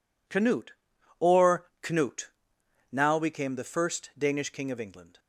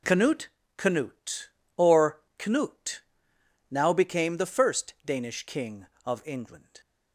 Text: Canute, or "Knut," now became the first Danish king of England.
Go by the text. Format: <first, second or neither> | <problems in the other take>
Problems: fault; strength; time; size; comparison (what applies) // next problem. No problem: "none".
first | says "Canute" twice; at 0.7 s // pauses between "or" and "Knut"; slight; at 2.2 s; 0.18 s long